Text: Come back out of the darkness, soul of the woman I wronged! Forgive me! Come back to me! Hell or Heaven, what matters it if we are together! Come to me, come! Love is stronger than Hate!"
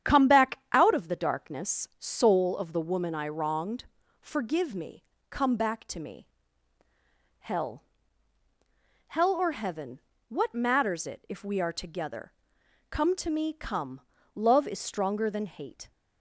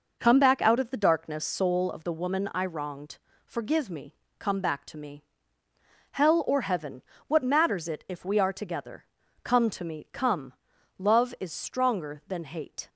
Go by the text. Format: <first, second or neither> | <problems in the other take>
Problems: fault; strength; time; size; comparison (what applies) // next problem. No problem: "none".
second | starts louder than the rest; strong; until 1.1 s; 9.5 dB // says "Hell" twice; at 9.0 s